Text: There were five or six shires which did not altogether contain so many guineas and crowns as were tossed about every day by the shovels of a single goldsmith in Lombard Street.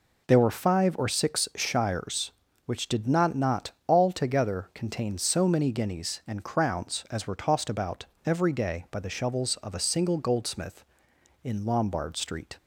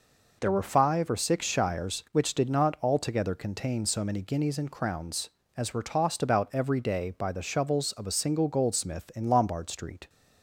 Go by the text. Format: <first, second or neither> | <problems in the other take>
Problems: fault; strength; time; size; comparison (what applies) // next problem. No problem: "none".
second | says "not" twice; at 3.3 s // pauses between "about" and "every"; slight; at 8.0 s; 0.18 s long